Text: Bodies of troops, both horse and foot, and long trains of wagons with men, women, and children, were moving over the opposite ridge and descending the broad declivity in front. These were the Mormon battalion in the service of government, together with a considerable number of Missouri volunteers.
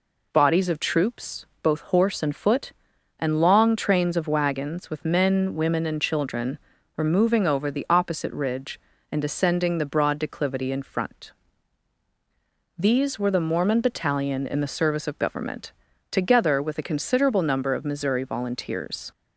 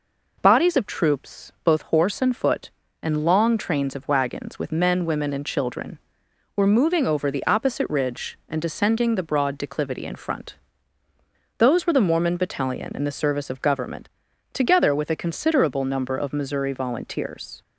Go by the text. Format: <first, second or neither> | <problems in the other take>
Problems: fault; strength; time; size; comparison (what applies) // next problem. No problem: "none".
first | says "Those" for "These"; at 11.5 s